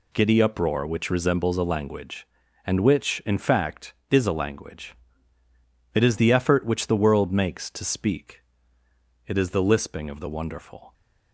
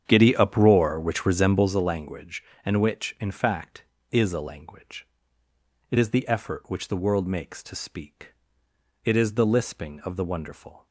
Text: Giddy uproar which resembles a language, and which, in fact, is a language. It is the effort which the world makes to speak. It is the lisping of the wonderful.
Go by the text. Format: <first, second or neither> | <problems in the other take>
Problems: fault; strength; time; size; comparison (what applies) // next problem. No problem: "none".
first | starts louder than the rest; strong; until 1.8 s; 8.5 dB